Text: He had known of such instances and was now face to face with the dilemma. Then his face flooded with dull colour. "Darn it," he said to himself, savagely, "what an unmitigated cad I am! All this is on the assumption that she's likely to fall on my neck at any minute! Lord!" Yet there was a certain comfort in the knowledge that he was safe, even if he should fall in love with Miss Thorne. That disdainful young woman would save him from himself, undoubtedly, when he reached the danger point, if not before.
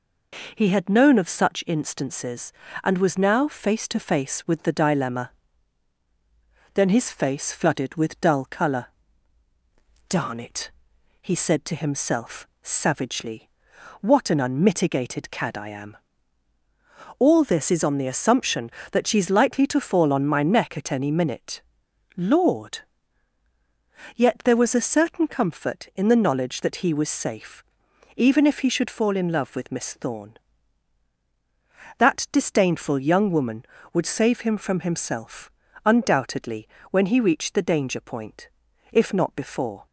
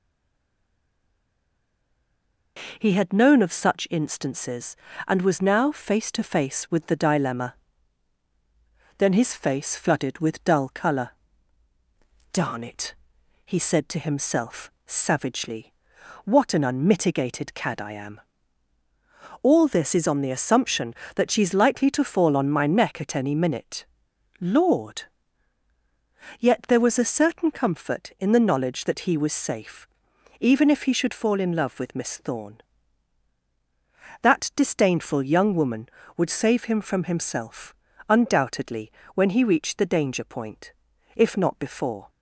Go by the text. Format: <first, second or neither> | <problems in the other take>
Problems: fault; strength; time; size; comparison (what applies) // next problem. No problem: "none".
first | stays silent before the first word; strong; until 2.5 s; 2.5 s long